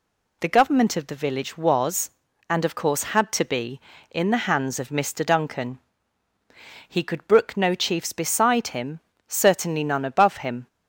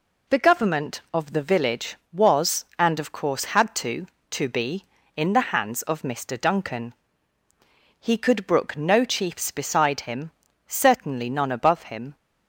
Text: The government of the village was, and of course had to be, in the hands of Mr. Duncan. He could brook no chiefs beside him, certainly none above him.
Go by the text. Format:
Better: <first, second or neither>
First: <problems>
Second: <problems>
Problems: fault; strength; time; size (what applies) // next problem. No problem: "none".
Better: first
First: none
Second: says "to" twice; at 4.3 s